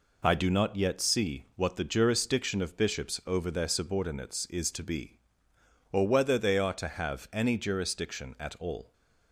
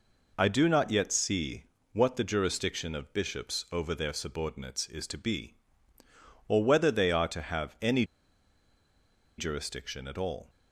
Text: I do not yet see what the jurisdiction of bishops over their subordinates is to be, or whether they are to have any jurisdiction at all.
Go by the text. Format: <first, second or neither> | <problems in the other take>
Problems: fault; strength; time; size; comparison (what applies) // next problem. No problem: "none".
first | pauses between "see" and "what"; slight; at 1.6 s; 0.30 s long // pauses between "any" and "jurisdiction"; strong; at 8.0 s; 1.3 s long